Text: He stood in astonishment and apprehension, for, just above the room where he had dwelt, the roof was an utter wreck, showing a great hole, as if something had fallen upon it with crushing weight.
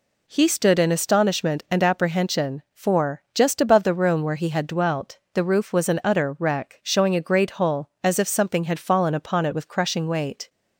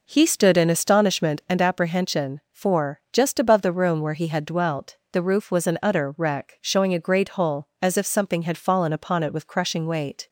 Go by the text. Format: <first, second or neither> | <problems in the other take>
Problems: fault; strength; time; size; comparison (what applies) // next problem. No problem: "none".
first | starts louder than the rest; noticeable; until 1.5 s; 4.5 dB